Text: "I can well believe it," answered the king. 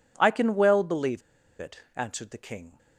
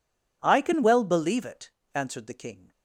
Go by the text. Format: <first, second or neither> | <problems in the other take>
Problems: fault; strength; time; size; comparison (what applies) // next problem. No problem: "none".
second | pauses between "believe" and "it"; at 1.1 s; 0.39 s long